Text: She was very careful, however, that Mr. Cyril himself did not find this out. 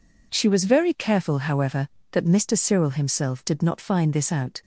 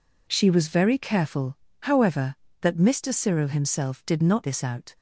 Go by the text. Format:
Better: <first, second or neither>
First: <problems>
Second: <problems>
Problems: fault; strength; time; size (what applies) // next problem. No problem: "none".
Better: first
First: none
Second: skips "find"; at 4.4 s